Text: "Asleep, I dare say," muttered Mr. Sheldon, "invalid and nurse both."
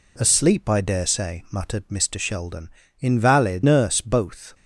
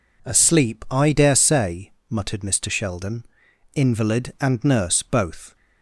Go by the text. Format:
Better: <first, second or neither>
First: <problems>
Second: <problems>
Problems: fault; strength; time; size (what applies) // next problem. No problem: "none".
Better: second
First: skips "and"; at 3.6 s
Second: none